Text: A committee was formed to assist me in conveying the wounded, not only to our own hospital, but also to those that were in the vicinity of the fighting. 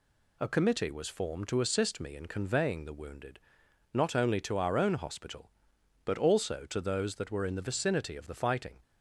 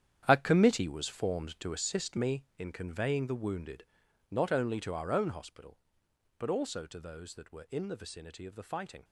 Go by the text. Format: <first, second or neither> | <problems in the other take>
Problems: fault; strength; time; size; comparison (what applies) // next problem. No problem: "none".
first | gets quieter; strong; throughout; 11 dB